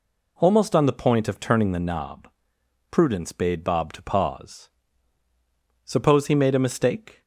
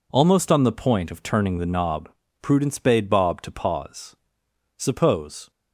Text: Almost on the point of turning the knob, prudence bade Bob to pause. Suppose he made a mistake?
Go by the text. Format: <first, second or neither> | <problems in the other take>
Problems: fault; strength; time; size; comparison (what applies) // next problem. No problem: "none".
first | stops before "he made a mistake"; at 5.5 s